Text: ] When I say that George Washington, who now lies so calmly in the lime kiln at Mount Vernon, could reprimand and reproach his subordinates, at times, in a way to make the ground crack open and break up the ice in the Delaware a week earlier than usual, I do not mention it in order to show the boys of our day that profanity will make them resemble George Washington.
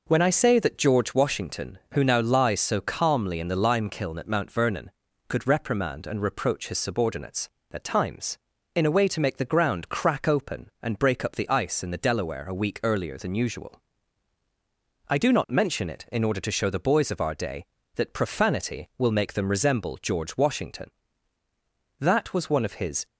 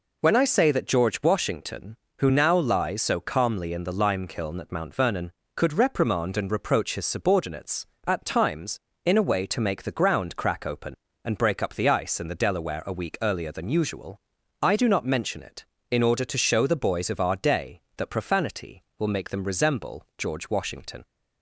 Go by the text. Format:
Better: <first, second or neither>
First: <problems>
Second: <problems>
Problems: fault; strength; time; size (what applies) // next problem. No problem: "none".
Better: second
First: goes on to say "That was one of his"; noticeable; from 21.9 s on; 1.0 s long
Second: none